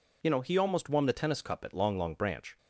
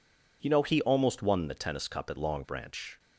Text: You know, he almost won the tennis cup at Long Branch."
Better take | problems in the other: second | says "Long" twice; at 1.9 s

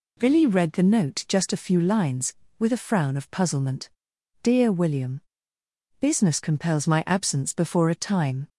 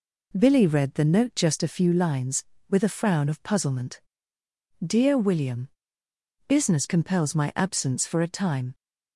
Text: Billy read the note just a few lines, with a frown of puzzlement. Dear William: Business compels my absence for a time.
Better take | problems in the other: second | says "before" for "for"; at 7.5 s

